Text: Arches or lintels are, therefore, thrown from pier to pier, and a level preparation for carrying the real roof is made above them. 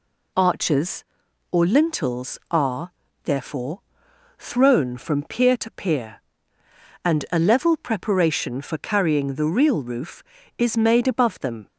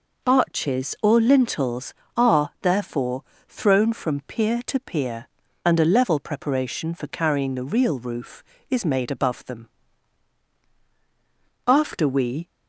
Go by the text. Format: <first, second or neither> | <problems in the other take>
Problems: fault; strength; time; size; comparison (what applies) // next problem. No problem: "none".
first | goes on to say "After we"; noticeable; from 11.6 s on; 0.80 s long